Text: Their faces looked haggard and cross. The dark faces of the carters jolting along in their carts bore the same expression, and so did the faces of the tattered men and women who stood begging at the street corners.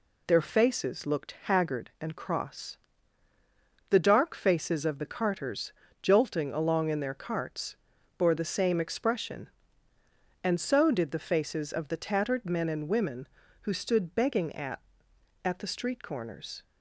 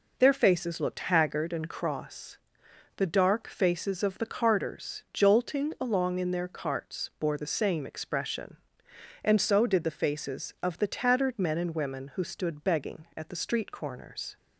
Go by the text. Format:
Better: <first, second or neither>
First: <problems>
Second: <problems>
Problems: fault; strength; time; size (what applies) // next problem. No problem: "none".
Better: second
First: pauses between "carters" and "jolting"; slight; at 5.7 s; 0.30 s long // pauses between "carts" and "bore"; at 7.7 s; 0.42 s long // says "at" twice; at 15.4 s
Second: none